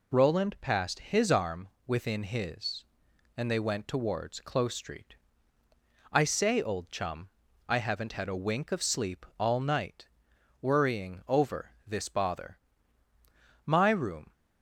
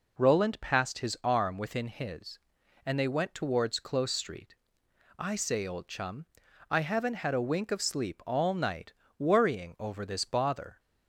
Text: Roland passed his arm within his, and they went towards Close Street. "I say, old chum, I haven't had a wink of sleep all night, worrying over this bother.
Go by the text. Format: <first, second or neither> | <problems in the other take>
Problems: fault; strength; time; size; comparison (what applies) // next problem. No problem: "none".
second | pauses between "arm" and "within"; slight; at 1.6 s; 0.18 s long // pauses between "over" and "this"; slight; at 11.7 s; 0.16 s long // goes on to say "My room"; noticeable; from 13.6 s on; 0.68 s long